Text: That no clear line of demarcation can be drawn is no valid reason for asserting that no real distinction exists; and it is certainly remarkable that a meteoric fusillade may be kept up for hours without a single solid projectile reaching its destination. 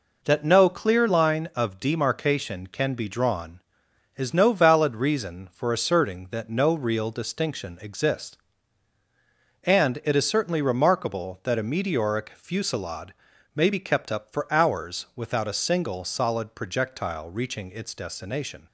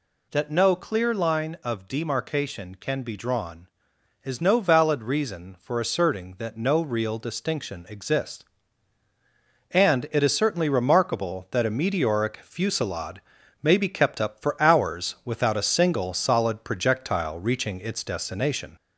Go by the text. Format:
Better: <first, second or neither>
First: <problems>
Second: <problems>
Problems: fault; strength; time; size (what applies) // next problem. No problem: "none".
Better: first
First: pauses between "fusillade" and "may"; at 13.1 s; 0.40 s long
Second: gets louder; slight; throughout; 2.5 dB // pauses between "fusillade" and "may"; at 13.2 s; 0.40 s long